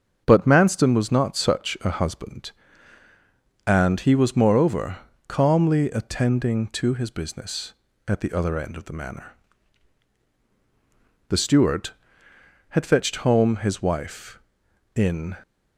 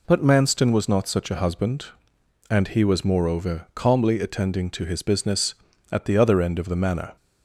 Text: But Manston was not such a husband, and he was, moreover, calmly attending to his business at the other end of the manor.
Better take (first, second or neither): second